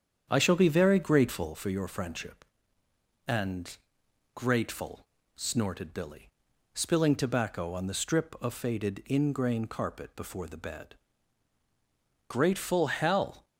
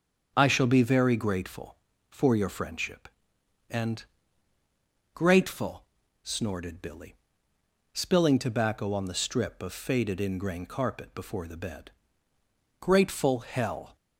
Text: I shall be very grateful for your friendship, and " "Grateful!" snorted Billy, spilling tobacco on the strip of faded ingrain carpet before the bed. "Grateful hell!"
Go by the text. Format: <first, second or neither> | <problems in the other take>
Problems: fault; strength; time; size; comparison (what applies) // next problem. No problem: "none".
second | starts louder than the rest; strong; until 1.5 s; 7.5 dB